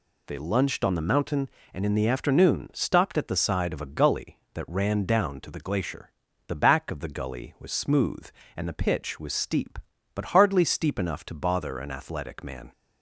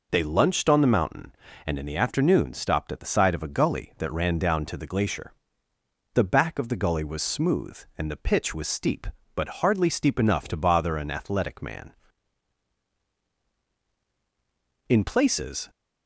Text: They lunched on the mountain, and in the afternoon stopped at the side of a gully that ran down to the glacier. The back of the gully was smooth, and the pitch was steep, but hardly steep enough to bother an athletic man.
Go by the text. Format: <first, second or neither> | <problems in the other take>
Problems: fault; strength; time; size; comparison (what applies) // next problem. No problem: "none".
first | goes on to say "In places"; noticeable; from 14.8 s on; 0.82 s long